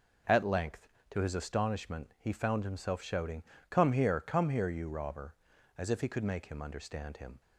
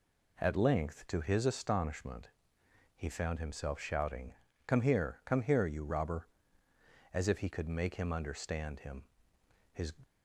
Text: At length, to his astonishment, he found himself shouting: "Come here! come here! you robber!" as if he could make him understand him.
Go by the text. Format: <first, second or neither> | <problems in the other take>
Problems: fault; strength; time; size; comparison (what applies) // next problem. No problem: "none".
first | goes on to say "His"; slight; from 9.7 s on; 0.22 s long